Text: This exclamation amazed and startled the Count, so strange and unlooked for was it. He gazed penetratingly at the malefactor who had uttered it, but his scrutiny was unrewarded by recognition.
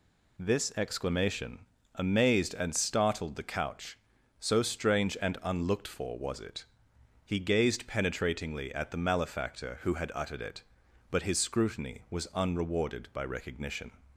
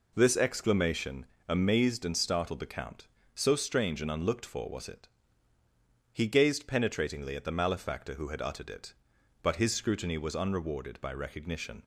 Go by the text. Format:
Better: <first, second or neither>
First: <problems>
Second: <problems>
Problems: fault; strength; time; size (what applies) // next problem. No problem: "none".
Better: second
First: pauses between "exclamation" and "amazed"; slight; at 1.6 s; 0.30 s long // says "Couch" for "Count"; at 3.4 s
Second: pauses between "exclamation" and "amazed"; slight; at 1.2 s; 0.24 s long